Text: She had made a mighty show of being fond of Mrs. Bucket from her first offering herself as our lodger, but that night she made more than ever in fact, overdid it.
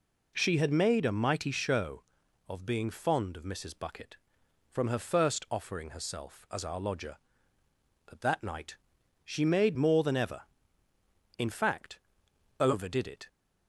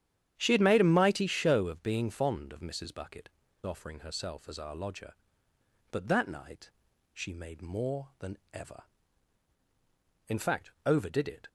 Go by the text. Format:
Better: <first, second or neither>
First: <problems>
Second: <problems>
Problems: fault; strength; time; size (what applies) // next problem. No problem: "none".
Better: first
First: pauses between "night" and "she"; noticeable; at 8.7 s; 0.50 s long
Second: starts louder than the rest; strong; until 1.3 s; 10 dB // skips "from her first"; at 3.4 s // pauses between "night" and "she"; at 6.6 s; 0.42 s long // pauses between "than" and "ever"; slight; at 8.3 s; 0.16 s long